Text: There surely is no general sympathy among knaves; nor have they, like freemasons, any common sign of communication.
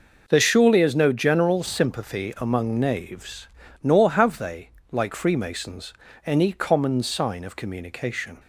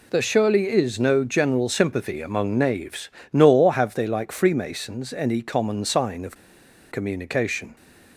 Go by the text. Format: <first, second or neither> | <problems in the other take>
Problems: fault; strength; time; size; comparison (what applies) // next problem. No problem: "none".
first | pauses between "of" and "communication"; noticeable; at 6.3 s; 0.56 s long